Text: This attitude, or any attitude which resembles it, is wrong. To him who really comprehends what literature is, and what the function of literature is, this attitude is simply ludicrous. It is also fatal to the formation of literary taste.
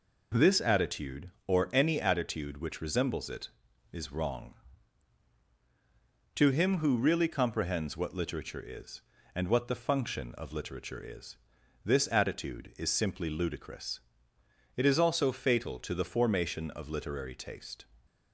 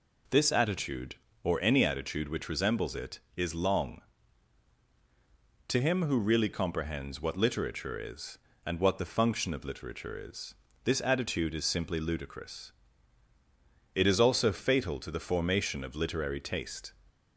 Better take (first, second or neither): first